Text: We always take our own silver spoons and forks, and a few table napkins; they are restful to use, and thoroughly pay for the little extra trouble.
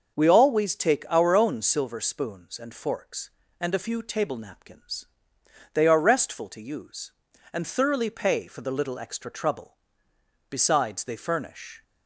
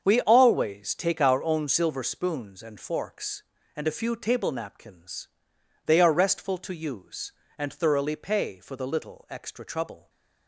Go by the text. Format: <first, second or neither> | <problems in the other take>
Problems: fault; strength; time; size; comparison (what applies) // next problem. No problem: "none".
second | starts louder than the rest; until 1.1 s; 6.5 dB; also in the second // goes on to say "Besides they furnish"; from 10.4 s on; 1.3 s long